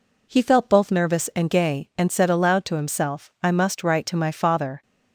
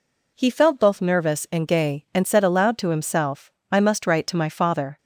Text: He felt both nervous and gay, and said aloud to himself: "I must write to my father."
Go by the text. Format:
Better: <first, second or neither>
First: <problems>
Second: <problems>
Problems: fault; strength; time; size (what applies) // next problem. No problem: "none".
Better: neither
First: none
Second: none